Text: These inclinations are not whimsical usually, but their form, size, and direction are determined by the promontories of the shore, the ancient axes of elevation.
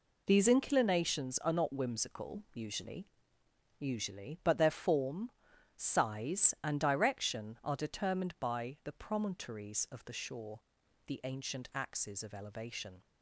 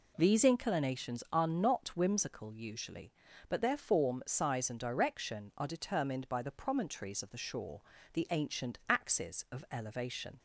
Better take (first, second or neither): second